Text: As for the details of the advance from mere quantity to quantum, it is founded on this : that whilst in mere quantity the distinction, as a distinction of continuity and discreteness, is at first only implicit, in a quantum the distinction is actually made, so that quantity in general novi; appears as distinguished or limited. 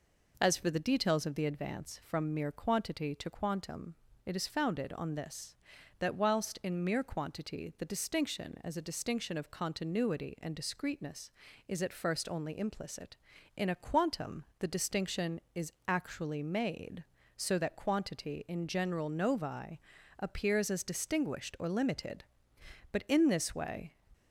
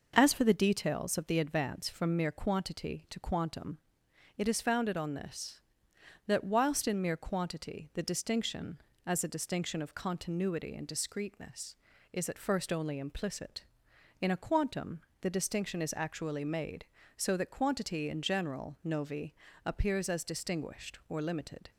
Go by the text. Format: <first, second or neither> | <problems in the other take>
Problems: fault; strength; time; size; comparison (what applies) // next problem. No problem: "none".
second | pauses between "quantum" and "the"; slight; at 14.4 s; 0.16 s long; slight in the second // pauses between "is" and "actually"; slight; at 15.7 s; 0.16 s long // goes on to say "But in this way"; noticeable; from 22.9 s on; 1.0 s long